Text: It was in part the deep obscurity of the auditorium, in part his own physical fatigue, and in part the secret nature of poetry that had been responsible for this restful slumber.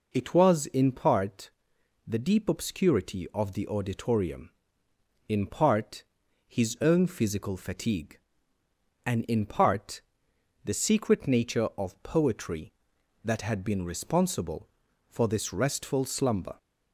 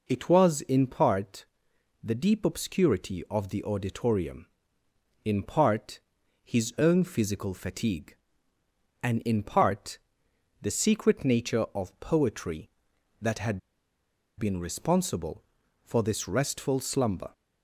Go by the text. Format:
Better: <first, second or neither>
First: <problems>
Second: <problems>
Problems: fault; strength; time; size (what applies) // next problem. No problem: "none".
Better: first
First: pauses between "part" and "the"; noticeable; at 1.4 s; 0.56 s long // pauses between "part" and "his"; at 6.0 s; 0.42 s long // pauses between "part" and "the"; noticeable; at 10.0 s; 0.62 s long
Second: pauses between "part" and "the"; noticeable; at 1.4 s; 0.58 s long // pauses between "part" and "his"; at 6.0 s; 0.42 s long // pauses between "part" and "the"; noticeable; at 9.9 s; 0.62 s long // pauses between "had" and "been"; noticeable; at 13.5 s; 0.78 s long